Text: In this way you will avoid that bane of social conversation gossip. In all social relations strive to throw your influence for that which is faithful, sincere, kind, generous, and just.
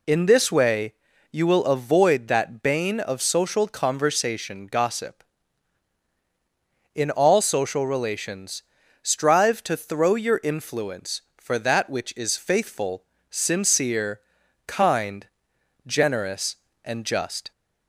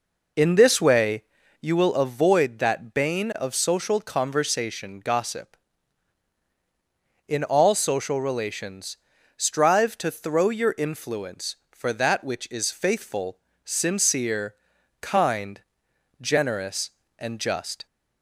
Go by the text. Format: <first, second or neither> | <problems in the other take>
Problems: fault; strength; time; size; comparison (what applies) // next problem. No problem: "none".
first | starts louder than the rest; noticeable; until 1.7 s; 4.5 dB // pauses between "way" and "you"; at 1.2 s; 0.40 s long; also in the first // pauses between "relations" and "strive"; at 8.9 s; 0.40 s long; also in the first